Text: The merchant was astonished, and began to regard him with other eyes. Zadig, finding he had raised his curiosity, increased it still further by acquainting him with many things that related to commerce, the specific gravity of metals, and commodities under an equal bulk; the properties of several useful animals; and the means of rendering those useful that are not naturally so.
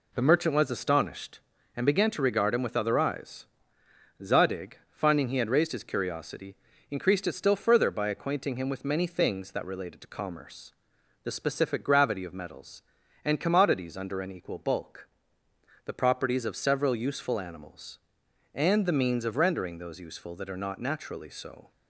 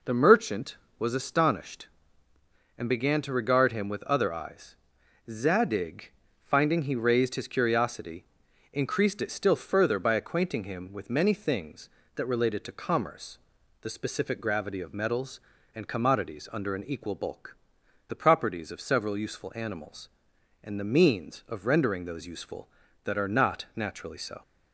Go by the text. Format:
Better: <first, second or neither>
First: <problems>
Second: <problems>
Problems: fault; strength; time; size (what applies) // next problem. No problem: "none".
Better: first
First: none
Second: skips "had"; at 6.9 s